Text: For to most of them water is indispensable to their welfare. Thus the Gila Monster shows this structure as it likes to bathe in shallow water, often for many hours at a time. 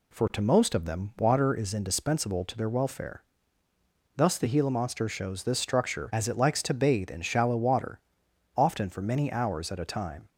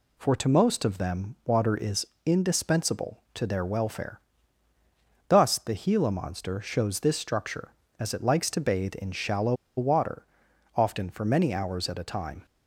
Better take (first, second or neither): first